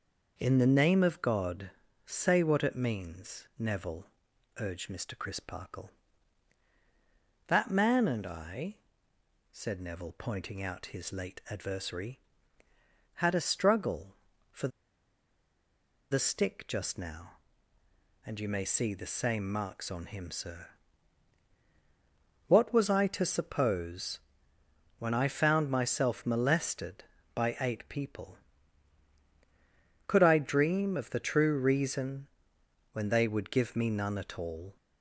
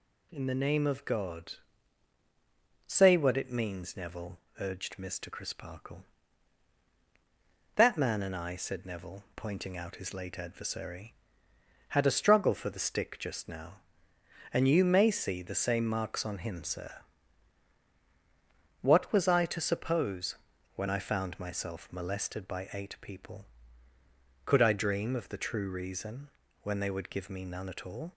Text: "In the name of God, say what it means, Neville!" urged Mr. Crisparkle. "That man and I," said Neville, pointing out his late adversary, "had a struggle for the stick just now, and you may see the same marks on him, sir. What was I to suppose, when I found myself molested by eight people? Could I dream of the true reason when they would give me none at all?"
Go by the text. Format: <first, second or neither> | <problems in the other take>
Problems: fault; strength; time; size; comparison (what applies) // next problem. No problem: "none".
second | pauses between "for" and "the"; strong; at 14.6 s; 1.4 s long // pauses between "reason" and "when"; noticeable; at 32.2 s; 0.64 s long; slight in the second